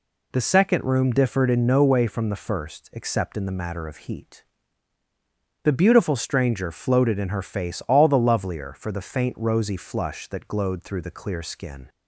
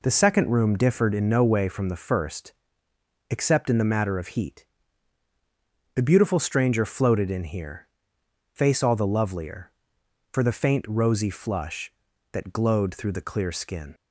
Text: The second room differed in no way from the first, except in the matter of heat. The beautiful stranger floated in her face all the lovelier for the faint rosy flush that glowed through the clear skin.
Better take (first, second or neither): first